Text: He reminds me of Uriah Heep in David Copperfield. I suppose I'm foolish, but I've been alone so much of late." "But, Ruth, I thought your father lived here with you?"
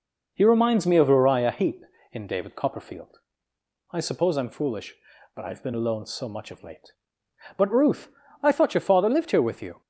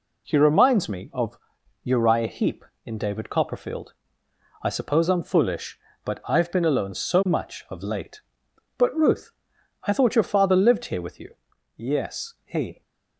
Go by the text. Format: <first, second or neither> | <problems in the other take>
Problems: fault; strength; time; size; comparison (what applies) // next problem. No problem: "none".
first | pauses between "of" and "Uriah"; noticeable; at 1.3 s; 0.46 s long // goes on to say "Yes he"; noticeable; from 11.7 s on; 1.0 s long